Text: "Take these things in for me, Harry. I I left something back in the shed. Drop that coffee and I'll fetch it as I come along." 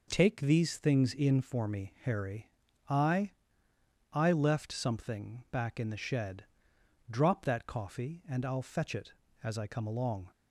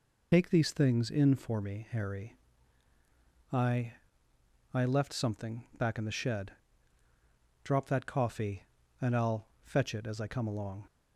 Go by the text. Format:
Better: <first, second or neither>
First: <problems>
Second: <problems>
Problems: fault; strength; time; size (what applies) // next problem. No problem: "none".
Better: first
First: pauses between "I" and "I"; noticeable; at 3.2 s; 0.82 s long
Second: loses the start of "Take"; at 0.3 s; 80 ms // pauses between "I" and "I"; noticeable; at 3.9 s; 0.80 s long // pauses between "I'll" and "fetch"; slight; at 9.4 s; 0.18 s long